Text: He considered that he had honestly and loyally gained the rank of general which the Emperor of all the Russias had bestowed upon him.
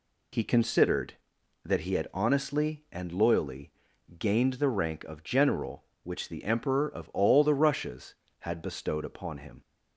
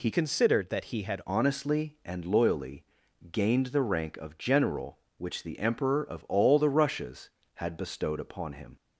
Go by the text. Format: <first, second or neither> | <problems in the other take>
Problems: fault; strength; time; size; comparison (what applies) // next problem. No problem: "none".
first | changes voice from "considered" to "had"; from 0.1 to 1.2 s; 1.1 s long // pauses between "loyally" and "gained"; noticeable; at 2.8 s; 0.48 s long; noticeable in the first